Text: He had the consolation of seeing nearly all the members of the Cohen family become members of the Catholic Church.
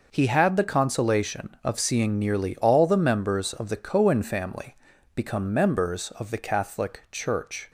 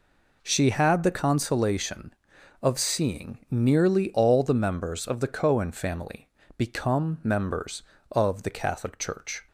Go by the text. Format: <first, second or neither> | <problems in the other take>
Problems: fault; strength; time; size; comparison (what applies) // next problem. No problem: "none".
first | says "She" for "He"; at 0.4 s // pauses between "family" and "become"; slight; at 6.2 s; 0.30 s long; also in the first